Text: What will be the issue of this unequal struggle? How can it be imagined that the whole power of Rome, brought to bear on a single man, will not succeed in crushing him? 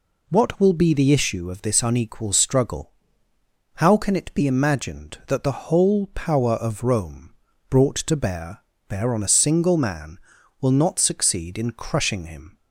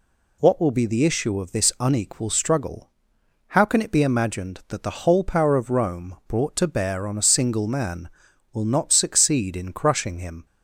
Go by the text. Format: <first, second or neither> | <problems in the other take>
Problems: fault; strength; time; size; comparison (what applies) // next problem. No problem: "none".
second | says "bear" twice; at 8.8 s